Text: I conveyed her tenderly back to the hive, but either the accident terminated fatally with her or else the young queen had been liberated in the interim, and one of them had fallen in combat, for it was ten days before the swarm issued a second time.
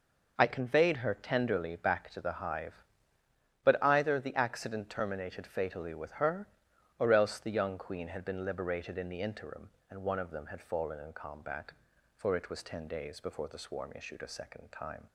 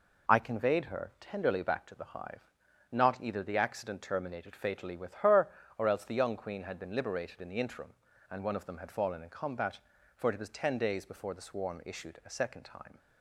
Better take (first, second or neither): first